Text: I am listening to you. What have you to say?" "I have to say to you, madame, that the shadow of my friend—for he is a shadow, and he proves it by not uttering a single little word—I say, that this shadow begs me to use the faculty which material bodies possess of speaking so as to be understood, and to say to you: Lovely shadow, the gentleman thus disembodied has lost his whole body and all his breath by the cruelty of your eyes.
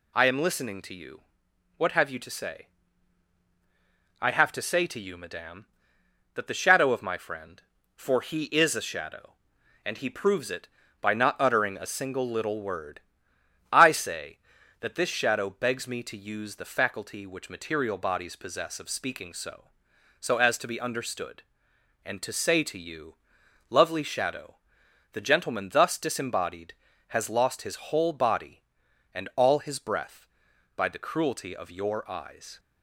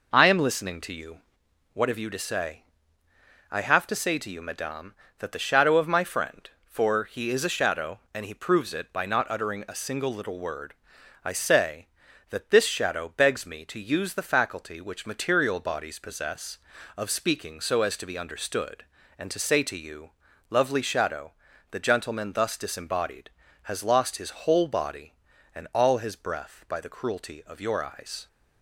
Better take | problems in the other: second | says "so" twice; at 20.2 s

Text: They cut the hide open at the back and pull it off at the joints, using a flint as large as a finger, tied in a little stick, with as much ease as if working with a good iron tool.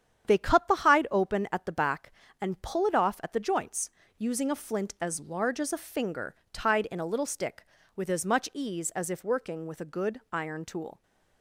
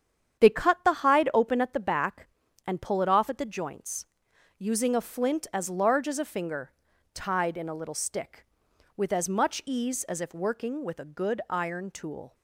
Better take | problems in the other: neither | starts louder than the rest; strong; the same in both

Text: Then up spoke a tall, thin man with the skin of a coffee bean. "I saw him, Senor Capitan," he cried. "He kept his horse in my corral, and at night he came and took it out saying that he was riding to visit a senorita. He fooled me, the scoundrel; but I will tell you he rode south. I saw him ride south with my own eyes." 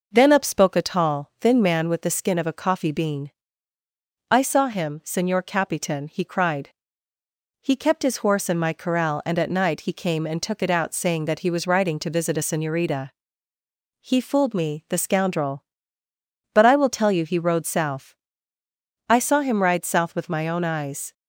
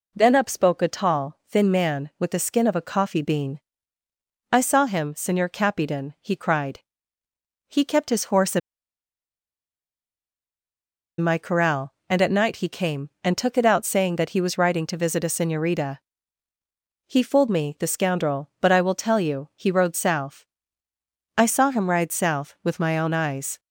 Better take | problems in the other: first | pauses between "in" and "my"; strong; at 8.5 s; 2.6 s long

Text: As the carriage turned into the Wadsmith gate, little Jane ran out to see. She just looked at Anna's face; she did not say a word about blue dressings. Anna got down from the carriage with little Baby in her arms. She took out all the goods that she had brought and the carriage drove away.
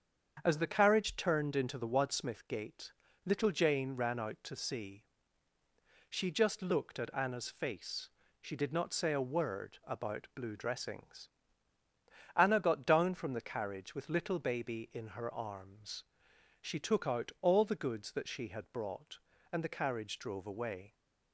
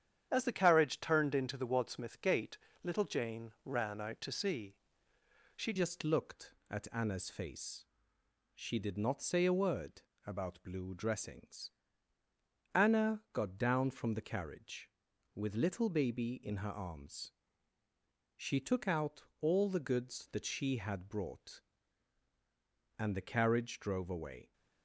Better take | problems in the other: first | starts louder than the rest; strong; until 1.3 s; 9 dB; strong in the first // changes voice at "just"; from 5.7 s on; 18.8 s long // pauses between "word" and "about"; slight; at 10.0 s; 0.24 s long // pauses between "out" and "all"; slight; at 19.2 s; 0.16 s long

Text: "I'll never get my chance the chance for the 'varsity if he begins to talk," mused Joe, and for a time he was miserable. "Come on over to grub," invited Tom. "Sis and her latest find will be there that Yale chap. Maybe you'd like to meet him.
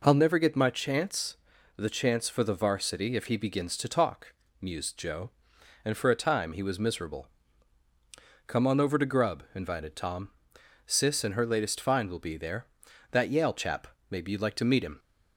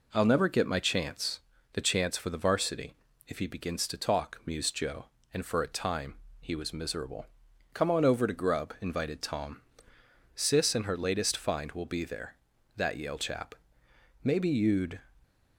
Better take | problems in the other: first | pauses between "chance" and "the"; slight; at 1.4 s; 0.32 s long; also in the first // pauses between "varsity" and "if"; slight; at 2.9 s; 0.34 s long // pauses between "time" and "he"; slight; at 6.1 s; 0.26 s long // stops before "like to meet him"; at 15.2 s

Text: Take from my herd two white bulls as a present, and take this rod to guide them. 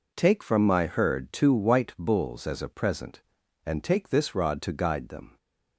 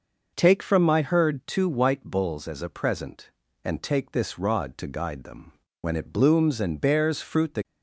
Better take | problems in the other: first | goes on to say "When it blooms and bears fruit the"; strong; from 5.8 s on; 1.8 s long

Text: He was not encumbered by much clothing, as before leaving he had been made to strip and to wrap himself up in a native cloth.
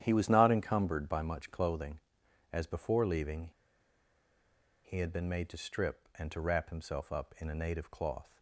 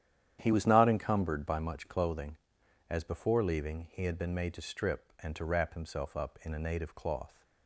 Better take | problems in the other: second | starts louder than the rest; strong; until 1.0 s; 10 dB; strong in the second // pauses between "leaving" and "he"; strong; at 3.5 s; 1.3 s long

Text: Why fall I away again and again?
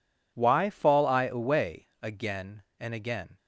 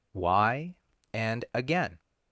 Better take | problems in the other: first | skips "fall I away again"; at 0.9 s

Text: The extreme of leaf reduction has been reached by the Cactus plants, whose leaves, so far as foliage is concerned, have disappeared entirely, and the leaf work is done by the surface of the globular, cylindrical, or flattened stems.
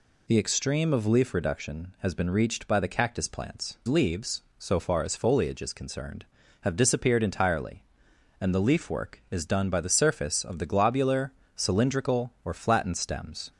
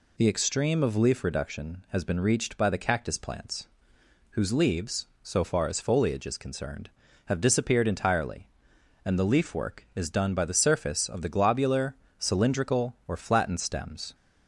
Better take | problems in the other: second | skips "whose"; at 3.8 s

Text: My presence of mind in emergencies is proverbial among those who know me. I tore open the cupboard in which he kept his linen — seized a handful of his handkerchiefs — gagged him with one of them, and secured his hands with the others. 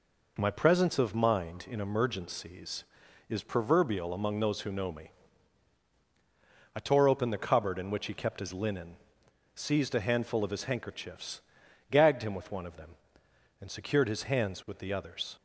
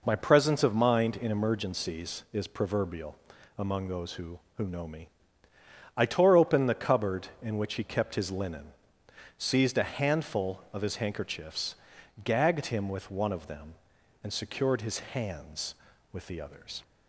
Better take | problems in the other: first | pauses between "proverbial" and "among"; at 3.1 s; 0.42 s long // says "who" twice; at 4.5 s

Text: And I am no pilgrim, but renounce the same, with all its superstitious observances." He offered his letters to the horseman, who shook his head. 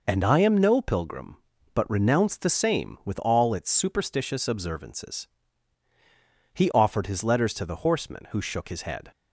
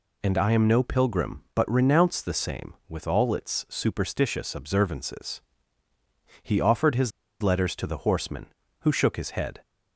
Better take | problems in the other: first | pauses between "his" and "letters"; slight; at 7.1 s; 0.31 s long

